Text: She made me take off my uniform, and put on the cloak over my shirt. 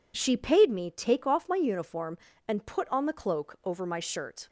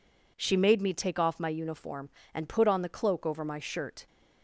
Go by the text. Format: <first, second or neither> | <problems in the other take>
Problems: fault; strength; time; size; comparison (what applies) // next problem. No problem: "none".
second | says "paid" for "made"; at 0.3 s